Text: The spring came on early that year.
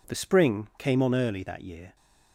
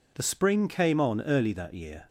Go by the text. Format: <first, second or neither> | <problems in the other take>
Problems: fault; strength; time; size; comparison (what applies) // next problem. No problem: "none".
neither | none